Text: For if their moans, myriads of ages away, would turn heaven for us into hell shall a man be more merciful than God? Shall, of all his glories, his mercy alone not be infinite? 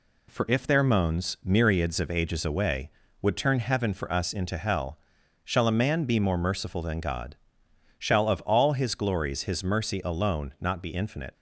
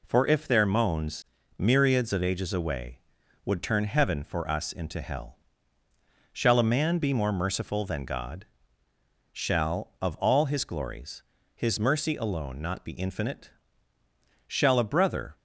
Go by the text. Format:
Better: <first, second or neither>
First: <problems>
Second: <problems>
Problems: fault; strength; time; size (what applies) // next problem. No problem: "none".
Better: first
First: pauses between "hell" and "shall"; at 4.9 s; 0.44 s long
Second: pauses between "hell" and "shall"; noticeable; at 5.3 s; 0.96 s long // goes on to say "Shall a brother"; noticeable; from 14.4 s on; 0.88 s long